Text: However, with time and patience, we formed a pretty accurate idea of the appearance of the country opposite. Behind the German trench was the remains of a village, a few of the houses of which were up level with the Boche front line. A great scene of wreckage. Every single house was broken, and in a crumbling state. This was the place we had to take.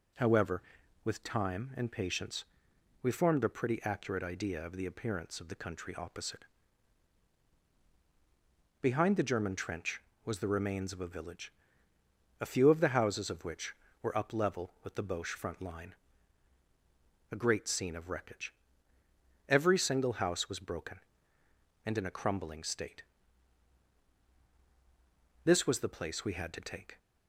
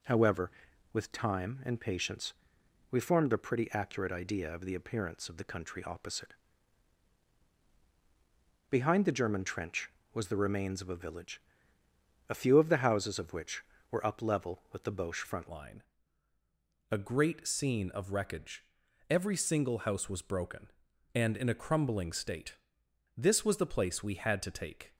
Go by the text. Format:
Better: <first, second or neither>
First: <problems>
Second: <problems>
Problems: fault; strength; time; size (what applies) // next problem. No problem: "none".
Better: first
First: none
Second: changes voice at "line"; from 15.4 s on; 9.5 s long